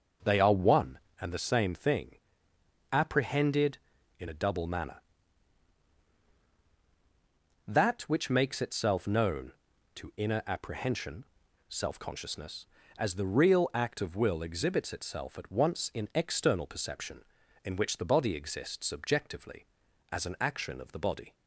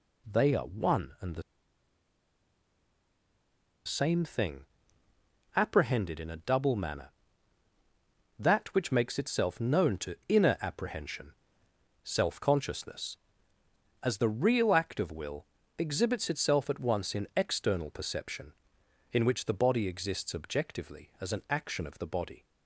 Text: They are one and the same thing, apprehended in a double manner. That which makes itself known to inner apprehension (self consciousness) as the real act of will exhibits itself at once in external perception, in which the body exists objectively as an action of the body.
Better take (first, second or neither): first